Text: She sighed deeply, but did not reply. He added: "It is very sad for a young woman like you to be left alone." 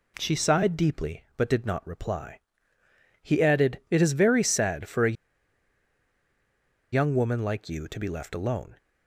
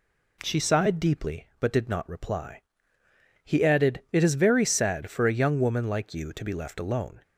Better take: second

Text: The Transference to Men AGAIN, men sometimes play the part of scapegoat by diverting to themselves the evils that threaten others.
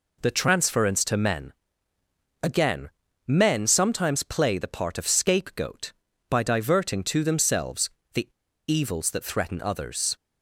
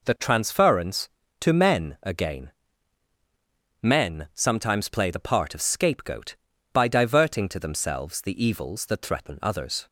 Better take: second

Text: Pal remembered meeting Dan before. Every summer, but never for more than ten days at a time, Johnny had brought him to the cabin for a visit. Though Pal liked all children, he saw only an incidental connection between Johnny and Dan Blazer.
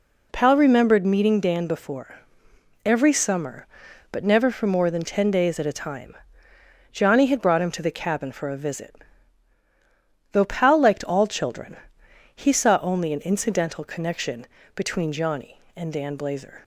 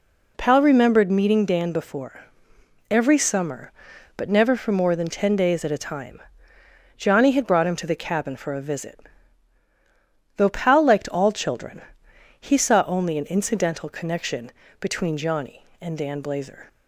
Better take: neither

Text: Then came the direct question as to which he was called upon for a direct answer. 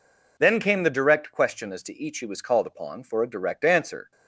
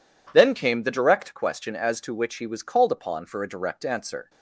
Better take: second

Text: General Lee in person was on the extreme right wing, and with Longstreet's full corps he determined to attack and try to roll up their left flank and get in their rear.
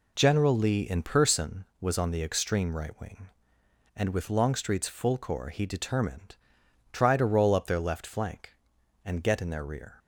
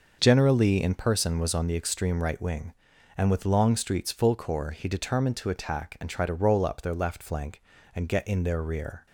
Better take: second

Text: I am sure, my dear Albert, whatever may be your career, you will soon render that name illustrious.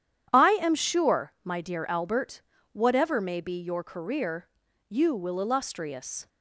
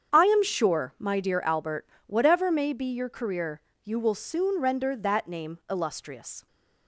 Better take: second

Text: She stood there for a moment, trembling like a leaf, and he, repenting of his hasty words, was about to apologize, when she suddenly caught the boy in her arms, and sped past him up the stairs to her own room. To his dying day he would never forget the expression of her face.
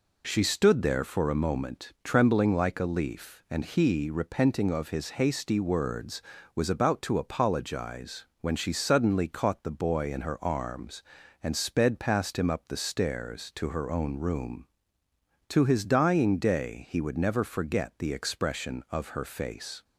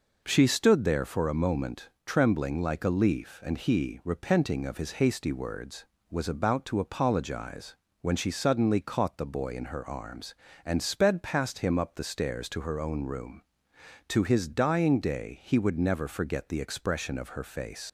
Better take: first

